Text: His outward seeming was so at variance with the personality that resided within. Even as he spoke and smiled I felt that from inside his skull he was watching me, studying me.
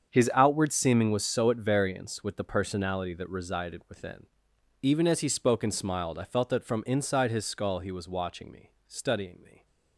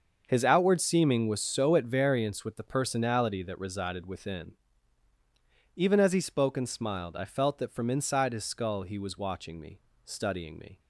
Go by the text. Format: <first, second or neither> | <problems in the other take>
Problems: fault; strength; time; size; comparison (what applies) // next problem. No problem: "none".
neither | starts louder than the rest; the same in both